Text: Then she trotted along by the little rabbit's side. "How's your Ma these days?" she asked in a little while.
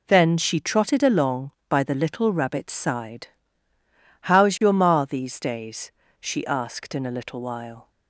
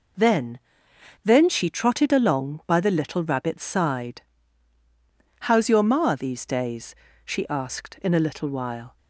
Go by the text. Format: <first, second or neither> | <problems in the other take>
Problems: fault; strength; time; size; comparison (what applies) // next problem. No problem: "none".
first | says "Then" twice; at 1.2 s